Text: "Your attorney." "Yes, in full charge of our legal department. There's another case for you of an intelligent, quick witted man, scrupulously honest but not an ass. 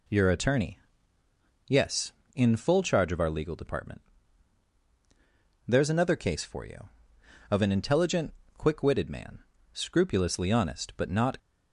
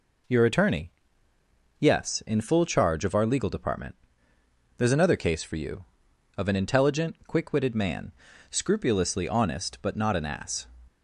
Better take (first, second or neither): second